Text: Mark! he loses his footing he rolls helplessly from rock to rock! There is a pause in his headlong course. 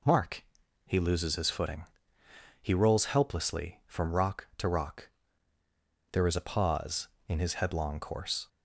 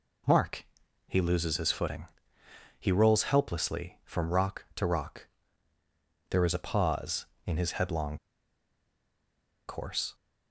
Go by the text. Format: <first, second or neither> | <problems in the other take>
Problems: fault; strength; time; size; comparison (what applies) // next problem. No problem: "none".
first | pauses between "footing" and "he"; noticeable; at 2.0 s; 0.74 s long; noticeable in the first // pauses between "headlong" and "course"; strong; at 8.1 s; 1.4 s long